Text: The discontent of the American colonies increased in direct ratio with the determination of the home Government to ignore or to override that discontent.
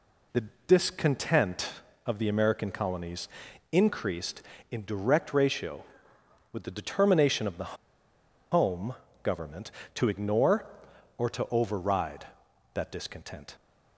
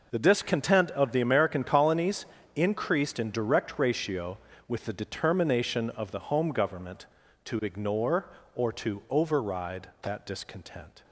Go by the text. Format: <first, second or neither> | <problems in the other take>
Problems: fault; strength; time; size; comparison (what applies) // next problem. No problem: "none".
second | pauses between "The" and "discontent"; slight; at 0.4 s; 0.24 s long // pauses between "colonies" and "increased"; at 3.2 s; 0.44 s long; slight in the second // pauses between "the" and "home"; noticeable; at 7.7 s; 0.75 s long // pauses between "home" and "Government"; slight; at 8.9 s; 0.28 s long